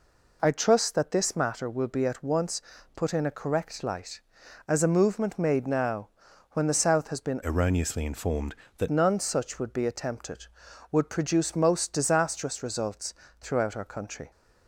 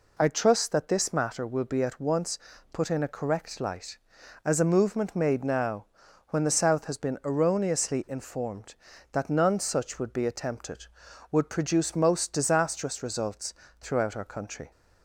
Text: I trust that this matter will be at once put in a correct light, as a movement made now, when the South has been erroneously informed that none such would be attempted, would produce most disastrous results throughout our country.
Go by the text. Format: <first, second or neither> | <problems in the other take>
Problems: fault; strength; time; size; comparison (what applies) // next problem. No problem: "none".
second | pauses between "once" and "put"; slight; at 2.6 s; 0.34 s long; slight in the second // changes voice from "erroneously" to "that"; from 7.4 to 8.8 s; 1.4 s long // pauses between "results" and "throughout"; slight; at 13.1 s; 0.26 s long; slight in the second